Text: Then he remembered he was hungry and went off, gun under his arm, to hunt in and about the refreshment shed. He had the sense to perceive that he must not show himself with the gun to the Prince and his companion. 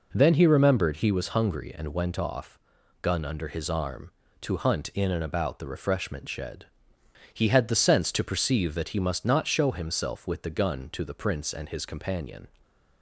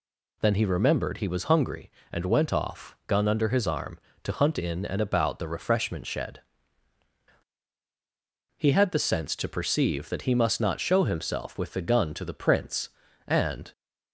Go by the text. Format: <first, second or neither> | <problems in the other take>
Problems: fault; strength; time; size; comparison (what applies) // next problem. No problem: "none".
first | stops before "his companion"; at 13.7 s